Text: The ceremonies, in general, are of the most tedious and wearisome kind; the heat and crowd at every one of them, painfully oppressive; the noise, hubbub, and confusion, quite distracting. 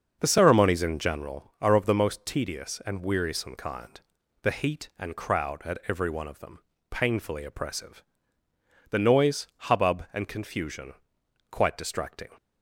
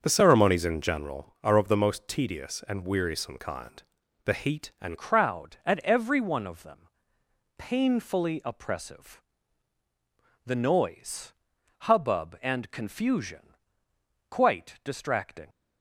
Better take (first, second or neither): first